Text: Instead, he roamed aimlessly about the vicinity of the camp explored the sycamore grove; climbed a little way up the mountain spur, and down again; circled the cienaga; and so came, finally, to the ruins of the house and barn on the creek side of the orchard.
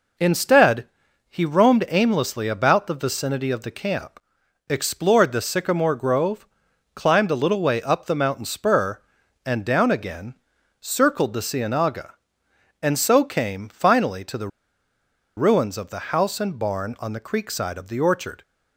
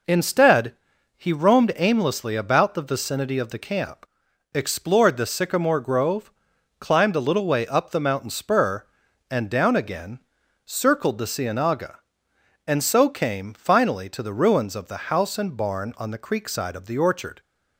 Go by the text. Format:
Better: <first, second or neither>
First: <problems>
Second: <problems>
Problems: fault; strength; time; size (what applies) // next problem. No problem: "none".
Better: second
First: pauses between "camp" and "explored"; noticeable; at 4.1 s; 0.50 s long // pauses between "the" and "ruins"; noticeable; at 14.4 s; 0.88 s long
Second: pauses between "camp" and "explored"; noticeable; at 4.0 s; 0.48 s long